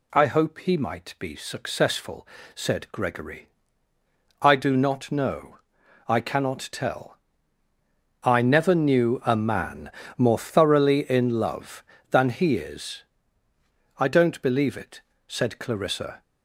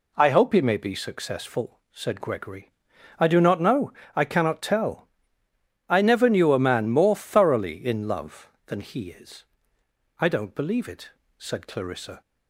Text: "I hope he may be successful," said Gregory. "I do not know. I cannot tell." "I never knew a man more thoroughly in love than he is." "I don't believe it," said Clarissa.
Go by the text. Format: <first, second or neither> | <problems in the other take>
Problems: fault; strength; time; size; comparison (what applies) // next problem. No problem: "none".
second | says "might" for "may"; at 0.7 s // pauses between "man" and "more"; slight; at 9.9 s; 0.26 s long